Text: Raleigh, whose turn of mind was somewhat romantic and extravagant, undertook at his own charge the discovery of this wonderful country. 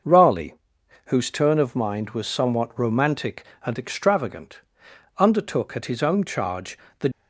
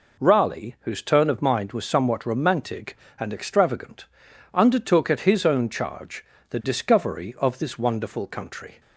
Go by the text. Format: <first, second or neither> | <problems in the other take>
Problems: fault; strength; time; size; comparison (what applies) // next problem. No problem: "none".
second | starts louder than the rest; noticeable; until 1.5 s; 6 dB // pauses between "charge" and "the"; slight; at 6.7 s; 0.22 s long; slight in the second // stops before "discovery of this wonderful country"; at 7.1 s